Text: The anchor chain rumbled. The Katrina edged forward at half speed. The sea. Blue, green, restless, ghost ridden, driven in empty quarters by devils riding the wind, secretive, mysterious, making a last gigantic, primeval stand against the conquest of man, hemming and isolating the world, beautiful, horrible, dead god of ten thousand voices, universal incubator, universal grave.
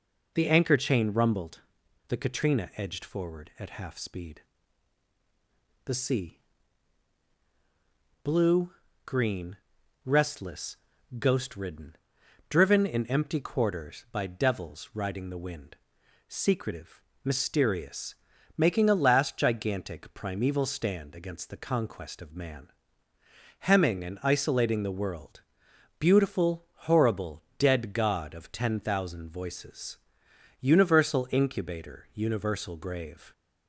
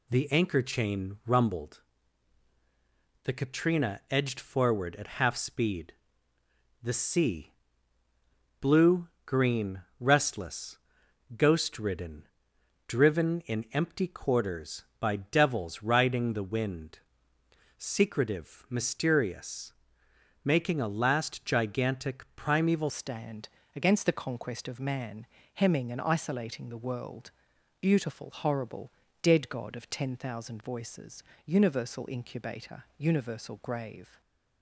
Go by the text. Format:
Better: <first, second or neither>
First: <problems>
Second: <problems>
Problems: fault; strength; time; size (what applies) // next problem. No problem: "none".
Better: first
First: none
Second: changes voice at "stand"; from 22.9 s on; 11.3 s long // pauses between "stand" and "against"; slight; at 23.4 s; 0.26 s long